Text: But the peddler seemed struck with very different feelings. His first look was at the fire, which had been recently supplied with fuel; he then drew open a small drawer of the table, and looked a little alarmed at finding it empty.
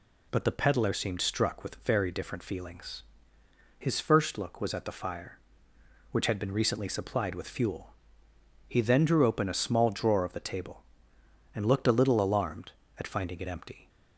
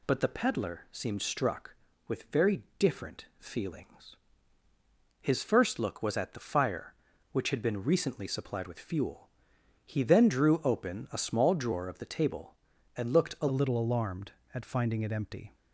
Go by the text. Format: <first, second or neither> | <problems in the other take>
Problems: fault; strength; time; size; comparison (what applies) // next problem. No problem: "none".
first | changes voice at "little"; from 13.5 s on; 2.0 s long